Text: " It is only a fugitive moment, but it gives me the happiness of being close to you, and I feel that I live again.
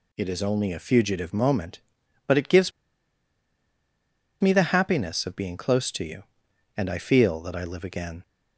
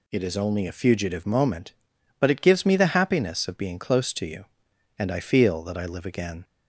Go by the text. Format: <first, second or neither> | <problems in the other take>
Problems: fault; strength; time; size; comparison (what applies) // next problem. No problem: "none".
second | pauses between "gives" and "me"; strong; at 2.7 s; 1.6 s long